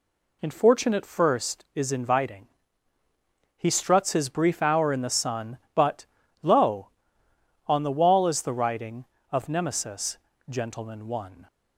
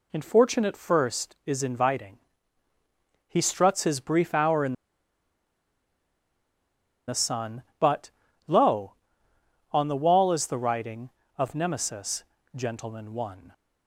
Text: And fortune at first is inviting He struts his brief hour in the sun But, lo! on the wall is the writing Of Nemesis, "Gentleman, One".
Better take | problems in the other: first | pauses between "inviting" and "He"; at 2.1 s; 1.1 s long; also in the first // pauses between "in" and "the"; strong; at 4.7 s; 2.3 s long

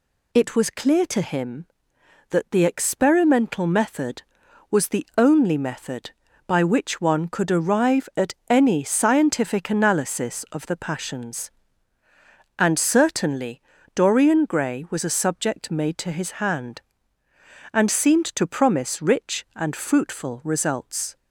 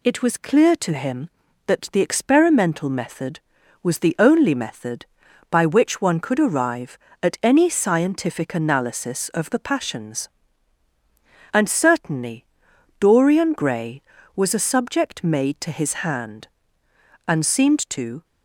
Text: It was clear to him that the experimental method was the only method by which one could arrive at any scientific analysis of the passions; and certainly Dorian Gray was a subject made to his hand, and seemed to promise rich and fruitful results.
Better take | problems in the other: first | pauses between "certainly" and "Dorian"; noticeable; at 12.4 s; 0.52 s long; slight in the first // stops before "promise rich and fruitful results"; at 18.2 s

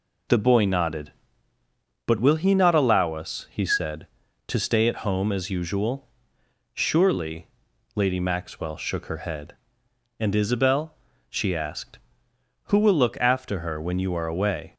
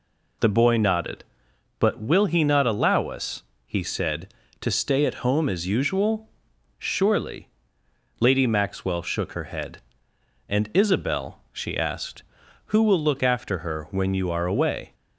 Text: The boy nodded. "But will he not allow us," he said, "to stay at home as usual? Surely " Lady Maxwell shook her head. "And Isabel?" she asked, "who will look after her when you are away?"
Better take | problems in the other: neither | none

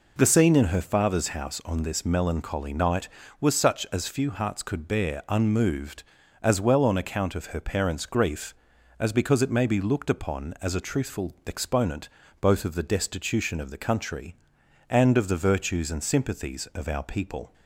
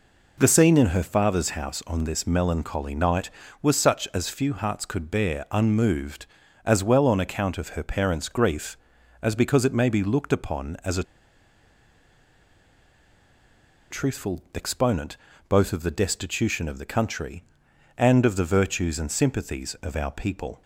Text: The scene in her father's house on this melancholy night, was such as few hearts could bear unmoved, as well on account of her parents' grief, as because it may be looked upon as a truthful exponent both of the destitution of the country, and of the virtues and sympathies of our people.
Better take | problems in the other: first | pauses between "a" and "truthful"; strong; at 11.0 s; 2.8 s long // pauses between "exponent" and "both"; slight; at 15.1 s; 0.32 s long; slight in the first

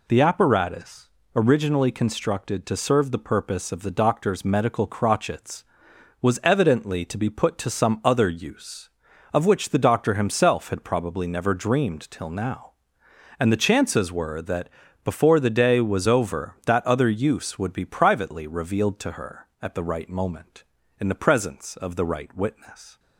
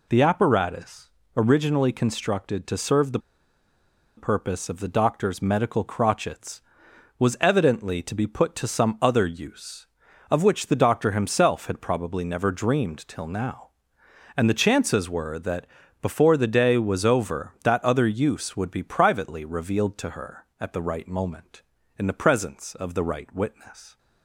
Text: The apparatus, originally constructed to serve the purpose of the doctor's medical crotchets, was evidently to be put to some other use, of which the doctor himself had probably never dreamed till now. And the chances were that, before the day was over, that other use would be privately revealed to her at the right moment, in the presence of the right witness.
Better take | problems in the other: first | pauses between "the" and "purpose"; noticeable; at 3.1 s; 0.97 s long

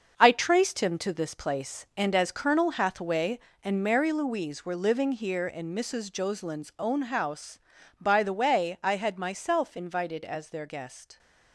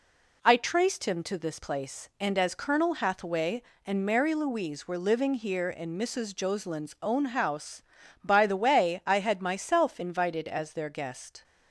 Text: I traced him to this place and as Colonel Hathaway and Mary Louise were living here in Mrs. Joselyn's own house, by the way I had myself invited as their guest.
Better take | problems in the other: second | gets quieter; strong; throughout; 8.5 dB

